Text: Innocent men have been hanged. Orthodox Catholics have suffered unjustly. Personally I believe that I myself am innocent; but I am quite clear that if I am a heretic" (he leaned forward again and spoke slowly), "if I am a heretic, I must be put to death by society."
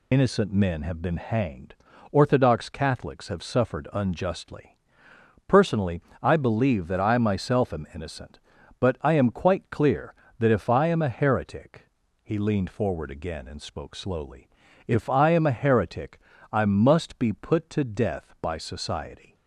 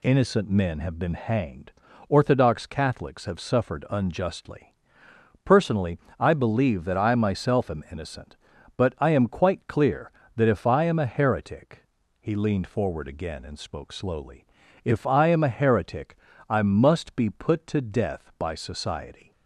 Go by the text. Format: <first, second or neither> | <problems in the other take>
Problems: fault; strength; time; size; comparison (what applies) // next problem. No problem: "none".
second | loses the start of "Innocent"; at 0.1 s; 55 ms // pauses between "Personally" and "I"; slight; at 6.0 s; 0.22 s long; slight in the second